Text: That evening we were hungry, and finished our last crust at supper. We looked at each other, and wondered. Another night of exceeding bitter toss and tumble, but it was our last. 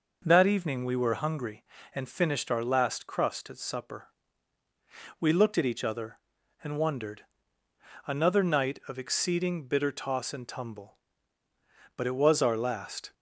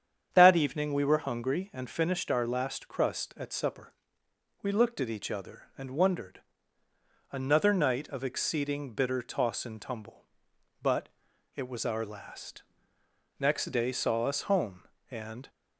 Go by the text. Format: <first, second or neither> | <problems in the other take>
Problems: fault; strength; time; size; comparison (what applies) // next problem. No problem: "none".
first | starts louder than the rest; strong; until 1.3 s; 8 dB // pauses between "but" and "it"; noticeable; at 11.0 s; 0.48 s long // goes on to say "Next day saw us home and"; strong; from 13.4 s on; 2.0 s long